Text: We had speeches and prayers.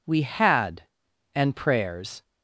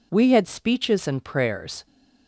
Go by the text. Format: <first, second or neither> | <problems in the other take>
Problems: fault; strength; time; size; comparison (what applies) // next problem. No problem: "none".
second | skips "speeches"; at 1.0 s